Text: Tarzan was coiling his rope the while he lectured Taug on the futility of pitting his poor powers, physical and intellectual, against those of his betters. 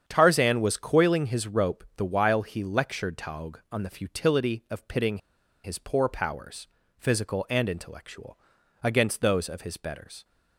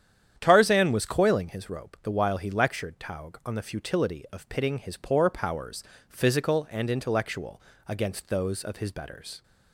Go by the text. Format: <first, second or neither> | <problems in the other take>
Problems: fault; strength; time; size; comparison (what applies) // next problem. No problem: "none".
second | starts louder than the rest; strong; until 1.0 s; 8 dB; strong in the second // pauses between "pitting" and "his"; at 5.1 s; 0.45 s long